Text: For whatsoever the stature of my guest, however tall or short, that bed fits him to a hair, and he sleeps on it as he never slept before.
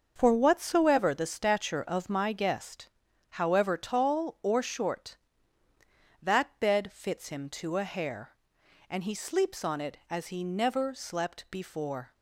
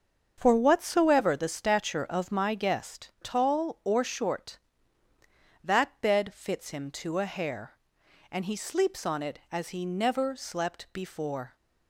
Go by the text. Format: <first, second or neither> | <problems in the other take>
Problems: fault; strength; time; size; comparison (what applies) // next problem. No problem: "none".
first | starts louder than the rest; until 1.3 s; 6.5 dB; also in the first // skips "however"; at 3.1 s